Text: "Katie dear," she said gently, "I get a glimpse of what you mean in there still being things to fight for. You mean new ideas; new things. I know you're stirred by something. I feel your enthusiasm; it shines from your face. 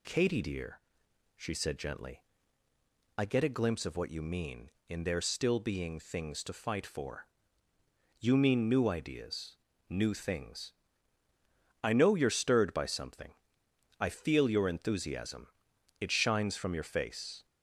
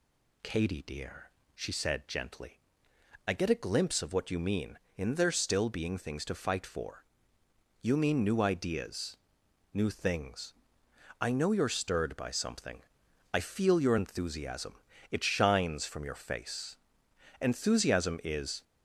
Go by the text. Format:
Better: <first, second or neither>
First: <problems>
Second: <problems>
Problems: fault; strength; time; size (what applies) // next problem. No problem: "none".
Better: first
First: none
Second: goes on to say "Enthusiasm is"; noticeable; from 17.4 s on; 1.2 s long